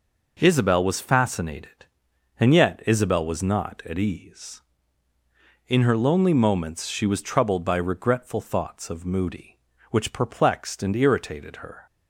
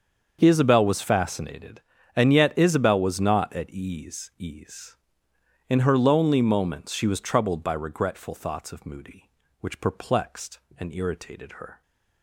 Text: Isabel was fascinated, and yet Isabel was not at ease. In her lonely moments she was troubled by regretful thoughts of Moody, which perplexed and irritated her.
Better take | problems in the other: first | starts louder than the rest; until 1.4 s; 6.5 dB // says "ease" twice; at 4.3 s

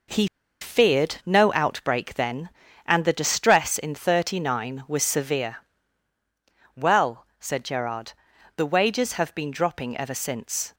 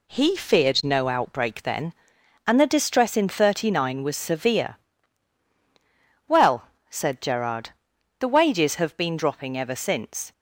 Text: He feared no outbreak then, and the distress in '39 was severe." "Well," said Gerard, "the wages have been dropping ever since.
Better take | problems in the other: second | pauses between "He" and "feared"; slight; at 0.2 s; 0.35 s long

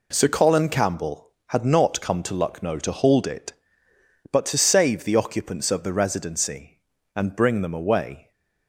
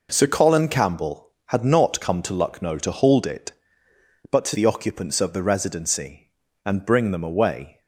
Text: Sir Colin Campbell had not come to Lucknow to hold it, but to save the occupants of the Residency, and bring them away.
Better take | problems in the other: first | skips "save"; at 4.5 s

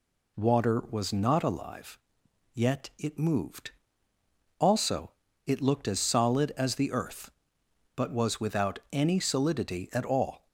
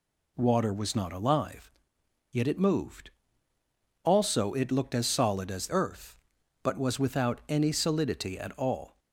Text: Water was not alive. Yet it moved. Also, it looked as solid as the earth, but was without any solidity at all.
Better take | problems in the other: first | skips "the"; at 5.6 s

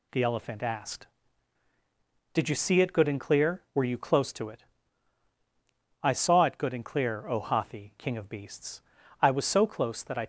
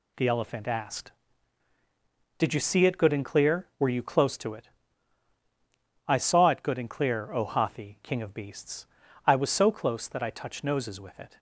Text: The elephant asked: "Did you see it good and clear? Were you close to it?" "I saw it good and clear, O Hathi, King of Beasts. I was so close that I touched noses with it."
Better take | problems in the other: second | stops before "touched noses with it"; at 10.2 s

